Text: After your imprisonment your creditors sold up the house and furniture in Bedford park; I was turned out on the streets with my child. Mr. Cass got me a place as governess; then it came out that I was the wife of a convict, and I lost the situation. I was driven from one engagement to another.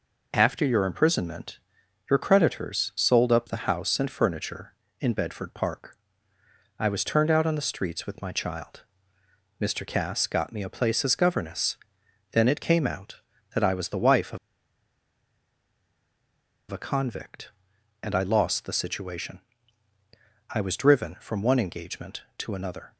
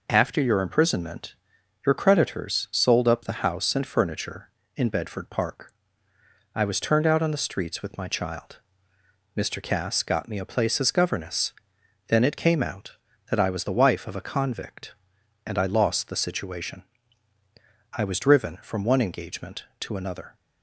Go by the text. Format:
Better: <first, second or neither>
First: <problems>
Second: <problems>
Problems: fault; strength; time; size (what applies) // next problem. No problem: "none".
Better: second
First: pauses between "imprisonment" and "your"; noticeable; at 1.5 s; 0.50 s long // pauses between "of" and "a"; strong; at 14.3 s; 2.3 s long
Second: pauses between "imprisonment" and "your"; noticeable; at 1.3 s; 0.50 s long